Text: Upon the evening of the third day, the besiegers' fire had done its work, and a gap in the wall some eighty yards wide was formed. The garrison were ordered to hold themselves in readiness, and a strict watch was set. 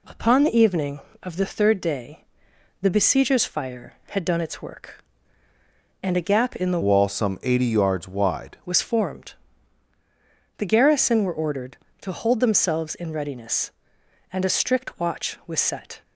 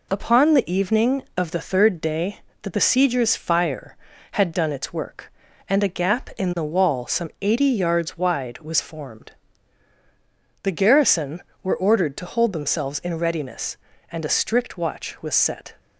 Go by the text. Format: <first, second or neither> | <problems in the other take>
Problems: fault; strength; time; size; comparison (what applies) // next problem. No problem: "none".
second | changes voice from "wall" to "wide"; from 6.8 to 8.5 s; 1.7 s long